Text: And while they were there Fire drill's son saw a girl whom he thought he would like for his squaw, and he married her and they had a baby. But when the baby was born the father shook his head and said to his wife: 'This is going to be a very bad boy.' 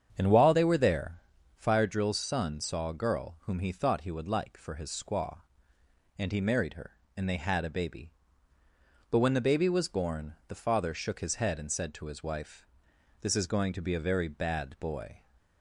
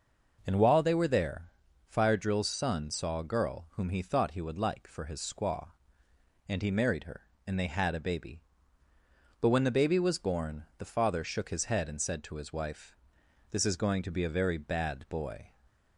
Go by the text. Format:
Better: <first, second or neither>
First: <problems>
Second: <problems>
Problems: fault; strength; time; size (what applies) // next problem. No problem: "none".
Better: second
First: starts louder than the rest; strong; until 1.8 s; 7.5 dB // pauses between "there" and "Fire"; at 1.1 s; 0.42 s long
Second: pauses between "there" and "Fire"; at 1.4 s; 0.42 s long